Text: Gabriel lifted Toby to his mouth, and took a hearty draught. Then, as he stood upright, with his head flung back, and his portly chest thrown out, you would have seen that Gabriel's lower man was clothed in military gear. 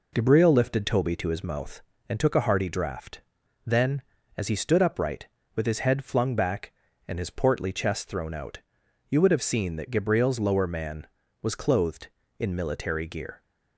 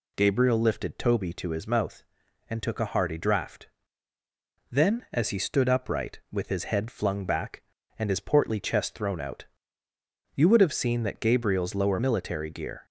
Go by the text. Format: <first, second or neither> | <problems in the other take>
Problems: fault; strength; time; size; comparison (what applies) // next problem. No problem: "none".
first | skips "man was clothed in"; at 12.0 s